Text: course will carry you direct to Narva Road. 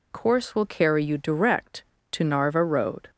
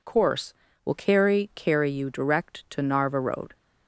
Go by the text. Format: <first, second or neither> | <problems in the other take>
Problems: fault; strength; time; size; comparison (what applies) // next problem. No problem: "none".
first | says "carry" twice; at 1.5 s